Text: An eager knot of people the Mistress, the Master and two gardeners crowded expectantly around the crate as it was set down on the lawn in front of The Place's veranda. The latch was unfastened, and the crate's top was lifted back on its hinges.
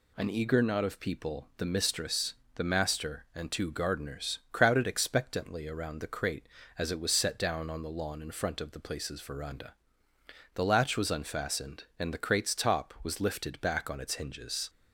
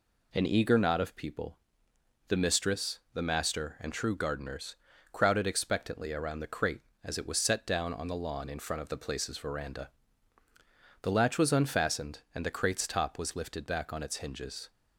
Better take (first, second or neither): first